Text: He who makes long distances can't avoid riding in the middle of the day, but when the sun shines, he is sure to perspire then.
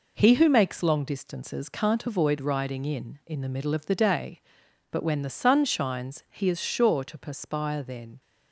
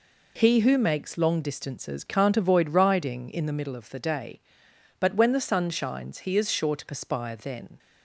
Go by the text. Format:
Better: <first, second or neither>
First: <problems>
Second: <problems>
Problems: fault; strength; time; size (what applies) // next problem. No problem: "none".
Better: second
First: says "in" twice; at 3.2 s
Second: none